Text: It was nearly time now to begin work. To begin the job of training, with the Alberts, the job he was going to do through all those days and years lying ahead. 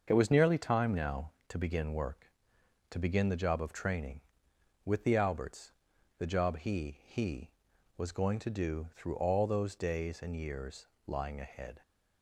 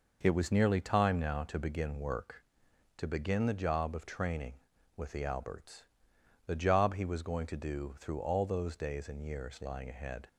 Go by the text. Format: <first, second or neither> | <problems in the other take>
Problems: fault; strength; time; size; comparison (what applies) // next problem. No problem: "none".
second | starts louder than the rest; until 1.0 s; 6.5 dB // says "he" twice; at 7.0 s // pauses between "years" and "lying"; slight; at 10.8 s; 0.20 s long